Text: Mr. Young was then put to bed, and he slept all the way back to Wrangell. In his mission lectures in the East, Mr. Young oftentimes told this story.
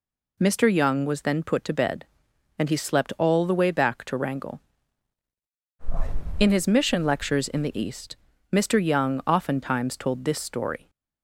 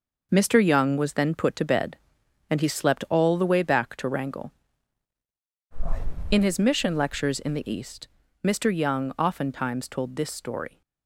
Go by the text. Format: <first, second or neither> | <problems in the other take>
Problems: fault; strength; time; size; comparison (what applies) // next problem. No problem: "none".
first | gets quieter; strong; throughout; 7.5 dB